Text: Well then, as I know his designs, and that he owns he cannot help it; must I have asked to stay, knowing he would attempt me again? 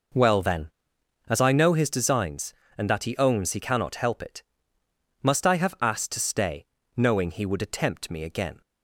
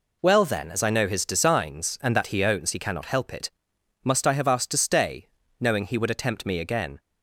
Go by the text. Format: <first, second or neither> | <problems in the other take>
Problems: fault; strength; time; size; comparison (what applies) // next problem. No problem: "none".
neither | none